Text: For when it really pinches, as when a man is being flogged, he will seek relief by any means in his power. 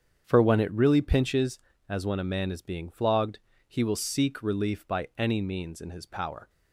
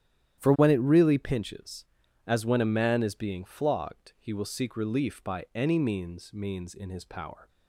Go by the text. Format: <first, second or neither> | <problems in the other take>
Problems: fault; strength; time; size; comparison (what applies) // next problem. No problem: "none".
first | starts louder than the rest; strong; until 1.4 s; 11 dB; strong in the first // says "means" twice; at 6.3 s